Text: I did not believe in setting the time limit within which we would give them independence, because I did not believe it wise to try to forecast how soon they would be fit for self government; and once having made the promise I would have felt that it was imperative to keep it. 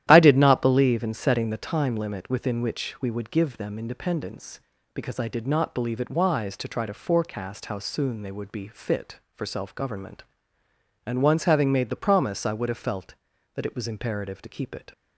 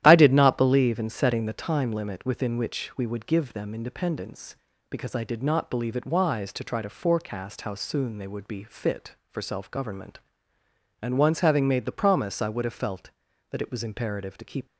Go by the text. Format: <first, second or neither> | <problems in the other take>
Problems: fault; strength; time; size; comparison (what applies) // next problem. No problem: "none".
first | starts louder than the rest; strong; until 1.0 s; 12 dB; strong in the first // stops before "it"; at 14.6 s